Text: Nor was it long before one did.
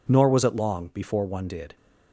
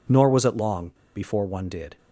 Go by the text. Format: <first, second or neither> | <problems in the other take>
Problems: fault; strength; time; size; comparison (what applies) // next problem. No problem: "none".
first | pauses between "long" and "before"; slight; at 0.8 s; 0.25 s long